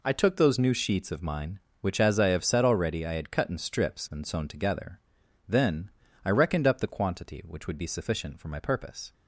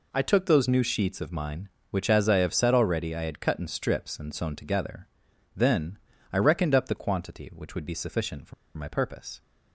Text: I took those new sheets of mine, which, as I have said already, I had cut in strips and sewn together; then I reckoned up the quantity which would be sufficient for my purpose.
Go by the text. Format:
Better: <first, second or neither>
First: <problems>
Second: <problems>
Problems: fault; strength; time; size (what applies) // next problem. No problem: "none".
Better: first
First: pauses between "then" and "I"; slight; at 5.9 s; 0.34 s long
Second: pauses between "then" and "I"; slight; at 5.9 s; 0.34 s long // pauses between "for" and "my"; slight; at 8.5 s; 0.23 s long